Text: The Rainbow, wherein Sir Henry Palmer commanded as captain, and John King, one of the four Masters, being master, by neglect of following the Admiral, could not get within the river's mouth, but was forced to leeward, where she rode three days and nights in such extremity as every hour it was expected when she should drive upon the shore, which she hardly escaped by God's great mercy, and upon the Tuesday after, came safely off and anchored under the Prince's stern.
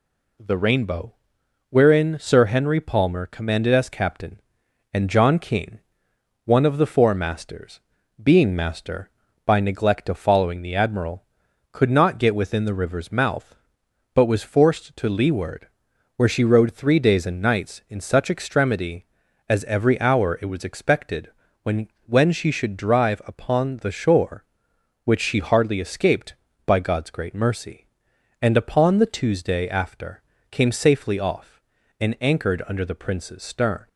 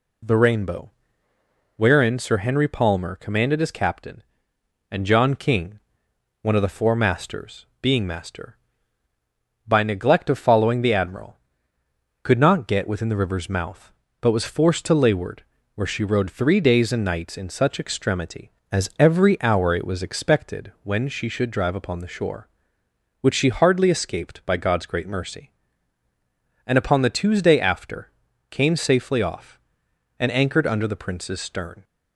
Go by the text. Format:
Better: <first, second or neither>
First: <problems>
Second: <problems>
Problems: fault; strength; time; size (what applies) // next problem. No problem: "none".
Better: second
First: pauses between "expected" and "when"; slight; at 21.2 s; 0.34 s long // says "when" twice; at 22.0 s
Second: none